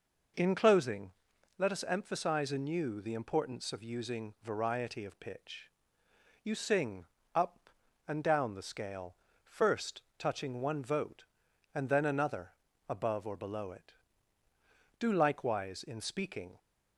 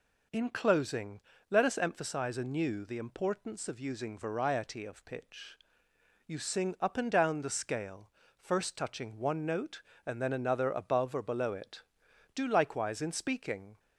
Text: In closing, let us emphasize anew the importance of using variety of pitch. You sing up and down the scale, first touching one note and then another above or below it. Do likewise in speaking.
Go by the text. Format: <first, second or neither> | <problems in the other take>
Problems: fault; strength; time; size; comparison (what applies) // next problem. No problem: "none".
second | pauses between "sing" and "up"; slight; at 7.0 s; 0.30 s long // pauses between "first" and "touching"; slight; at 10.0 s; 0.16 s long // says "vote" for "note"; at 10.8 s // pauses between "another" and "above"; at 12.4 s; 0.40 s long